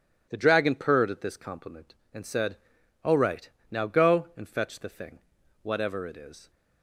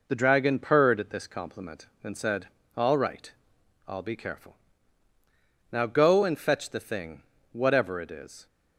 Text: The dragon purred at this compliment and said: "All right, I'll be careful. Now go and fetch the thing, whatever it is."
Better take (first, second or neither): second